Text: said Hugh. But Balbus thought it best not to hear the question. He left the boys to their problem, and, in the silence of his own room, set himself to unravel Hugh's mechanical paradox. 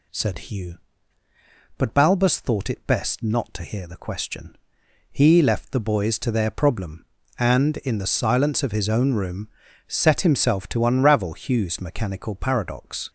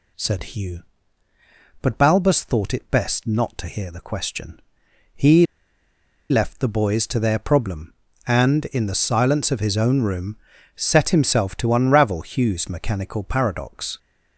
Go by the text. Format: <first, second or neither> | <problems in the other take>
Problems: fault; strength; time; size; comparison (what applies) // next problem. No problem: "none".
first | pauses between "He" and "left"; noticeable; at 5.4 s; 0.84 s long